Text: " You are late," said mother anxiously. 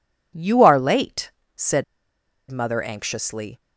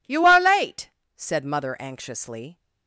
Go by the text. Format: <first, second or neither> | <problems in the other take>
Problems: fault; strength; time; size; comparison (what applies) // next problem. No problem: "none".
second | pauses between "said" and "mother"; noticeable; at 1.8 s; 0.66 s long